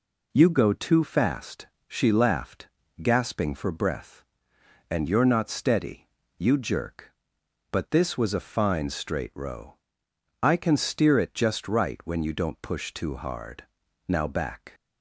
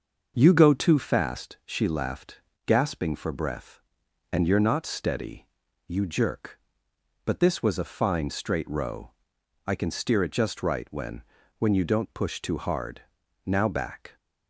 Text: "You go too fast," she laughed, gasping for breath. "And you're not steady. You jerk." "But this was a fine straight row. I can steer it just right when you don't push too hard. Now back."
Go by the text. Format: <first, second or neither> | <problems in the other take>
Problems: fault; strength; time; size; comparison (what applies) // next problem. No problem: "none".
first | starts louder than the rest; until 1.3 s; 6 dB // says "when" twice; at 11.6 s